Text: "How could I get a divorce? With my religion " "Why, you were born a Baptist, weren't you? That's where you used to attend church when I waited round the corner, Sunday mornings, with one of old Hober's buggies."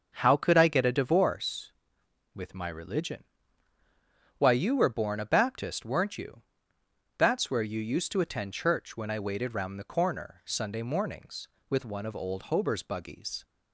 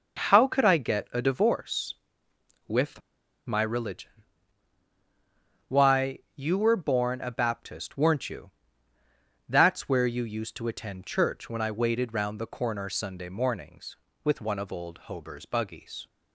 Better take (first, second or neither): first